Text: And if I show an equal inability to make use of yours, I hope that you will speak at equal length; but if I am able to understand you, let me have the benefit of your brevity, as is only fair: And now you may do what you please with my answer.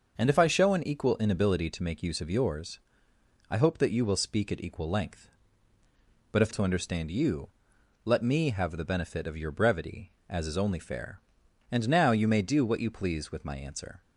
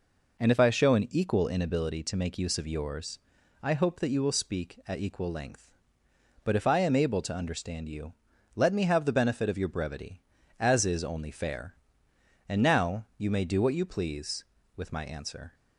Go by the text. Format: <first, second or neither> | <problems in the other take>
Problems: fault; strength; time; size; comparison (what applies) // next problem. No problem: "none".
second | starts louder than the rest; until 1.2 s; 6 dB // skips "I am able"; at 6.5 s